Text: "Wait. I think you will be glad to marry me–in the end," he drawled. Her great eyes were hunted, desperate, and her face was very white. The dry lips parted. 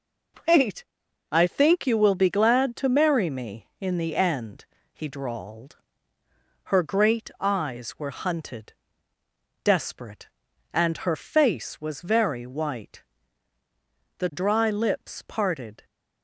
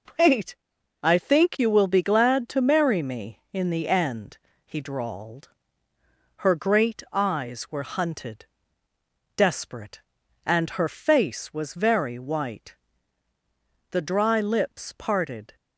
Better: neither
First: none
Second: none

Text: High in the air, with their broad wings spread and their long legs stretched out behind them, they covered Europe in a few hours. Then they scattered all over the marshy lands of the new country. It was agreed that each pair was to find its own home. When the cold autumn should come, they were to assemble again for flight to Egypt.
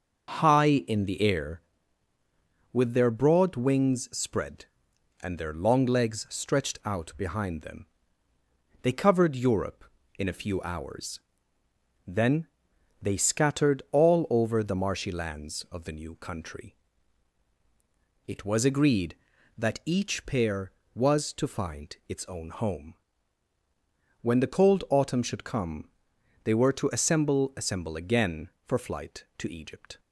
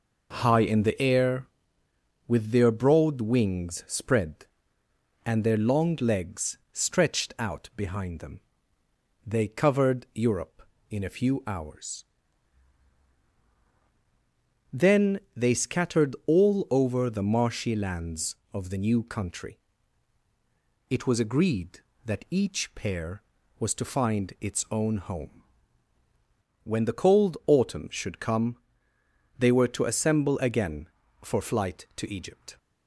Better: second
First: starts louder than the rest; noticeable; until 1.4 s; 6 dB // pauses between "Then" and "they"; noticeable; at 12.4 s; 0.54 s long // says "assemble" twice; at 27.5 s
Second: pauses between "Then" and "they"; slight; at 15.1 s; 0.16 s long

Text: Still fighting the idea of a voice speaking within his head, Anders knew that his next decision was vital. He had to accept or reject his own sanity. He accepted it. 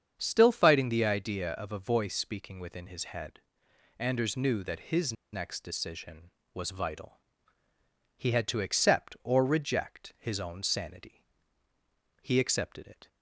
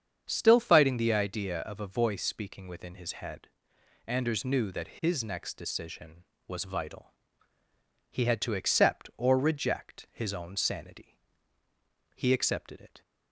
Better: second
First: starts louder than the rest; strong; until 1.1 s; 7.5 dB // pauses between "his" and "next"; slight; at 5.1 s; 0.20 s long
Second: starts louder than the rest; strong; until 1.2 s; 7.5 dB

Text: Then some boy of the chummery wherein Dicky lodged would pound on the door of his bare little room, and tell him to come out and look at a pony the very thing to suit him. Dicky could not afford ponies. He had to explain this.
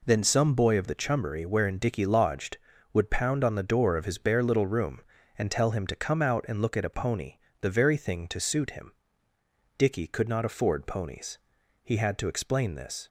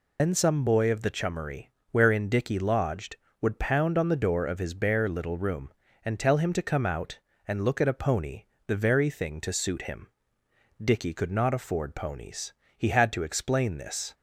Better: first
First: pauses between "pony" and "the"; slight; at 7.3 s; 0.24 s long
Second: loses the start of "Then"; at 0.1 s; 100 ms // pauses between "chummery" and "wherein"; slight; at 1.6 s; 0.22 s long // pauses between "pony" and "the"; slight; at 8.4 s; 0.24 s long

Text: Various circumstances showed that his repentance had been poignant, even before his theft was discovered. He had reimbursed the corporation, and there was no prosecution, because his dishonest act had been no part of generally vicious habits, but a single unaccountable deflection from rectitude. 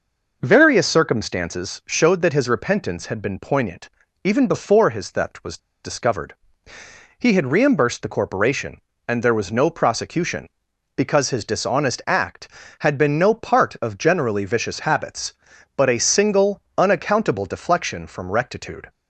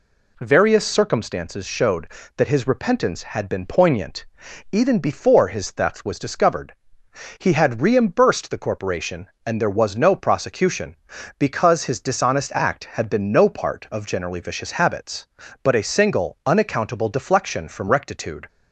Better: second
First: pauses between "was" and "discovered"; slight; at 5.5 s; 0.25 s long // pauses between "single" and "unaccountable"; slight; at 16.6 s; 0.16 s long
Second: none

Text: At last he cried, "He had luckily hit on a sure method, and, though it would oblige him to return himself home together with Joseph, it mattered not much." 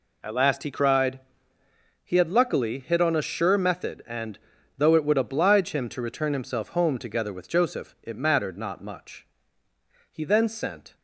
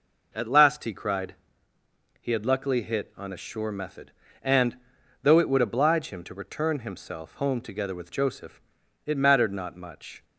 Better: second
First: goes on to say "He then sent"; noticeable; from 10.1 s on; 0.84 s long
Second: none

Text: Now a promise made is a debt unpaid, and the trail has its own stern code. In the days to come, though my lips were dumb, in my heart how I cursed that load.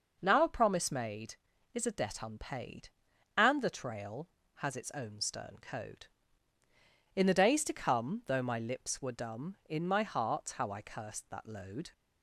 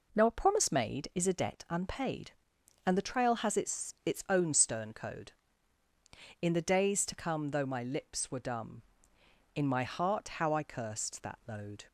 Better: first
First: none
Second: says "its" twice; at 4.0 s

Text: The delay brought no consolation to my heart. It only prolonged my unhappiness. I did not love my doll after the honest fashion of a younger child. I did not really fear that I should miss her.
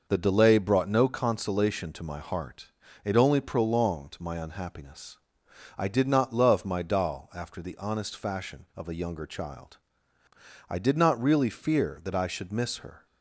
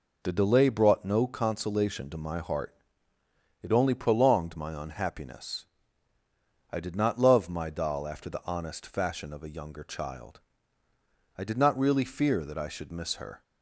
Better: neither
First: none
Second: none

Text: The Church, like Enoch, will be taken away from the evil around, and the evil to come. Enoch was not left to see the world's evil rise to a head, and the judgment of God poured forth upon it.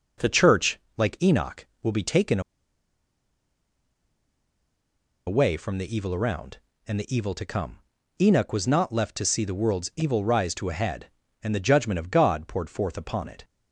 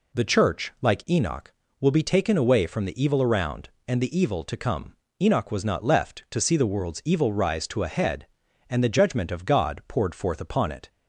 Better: second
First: pauses between "taken" and "away"; strong; at 2.4 s; 2.8 s long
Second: none

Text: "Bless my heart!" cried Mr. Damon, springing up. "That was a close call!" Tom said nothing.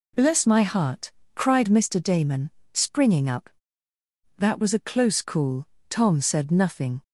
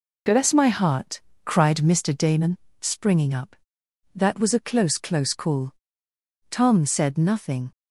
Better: first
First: none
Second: says "close" twice; at 4.9 s

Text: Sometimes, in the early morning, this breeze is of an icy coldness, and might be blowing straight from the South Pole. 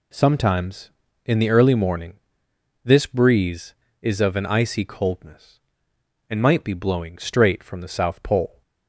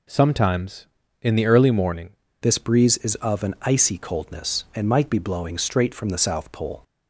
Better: first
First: none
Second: changes voice at "this"; from 2.4 s on; 4.4 s long

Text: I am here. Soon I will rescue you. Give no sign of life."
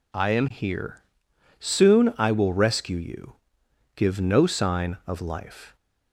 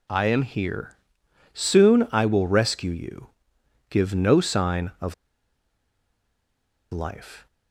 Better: first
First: none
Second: pauses between "of" and "life"; strong; at 5.1 s; 1.7 s long

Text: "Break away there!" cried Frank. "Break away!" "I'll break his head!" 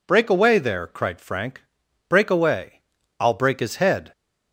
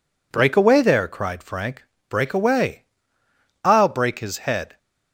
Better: neither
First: none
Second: none

